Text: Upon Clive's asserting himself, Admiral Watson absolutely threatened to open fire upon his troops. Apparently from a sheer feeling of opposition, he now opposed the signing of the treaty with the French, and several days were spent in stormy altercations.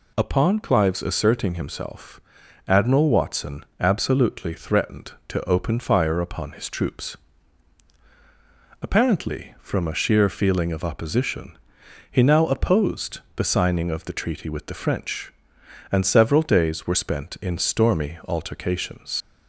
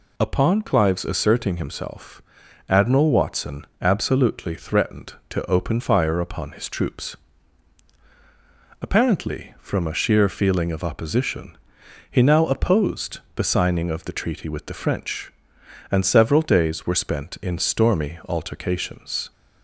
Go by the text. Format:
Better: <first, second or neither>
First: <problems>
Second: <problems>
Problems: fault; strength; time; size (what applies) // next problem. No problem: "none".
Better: second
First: pauses between "opposed" and "the"; slight; at 13.2 s; 0.16 s long // leaves "altercations" unfinished; at 19.2 s; 100 ms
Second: pauses between "opposed" and "the"; slight; at 13.2 s; 0.16 s long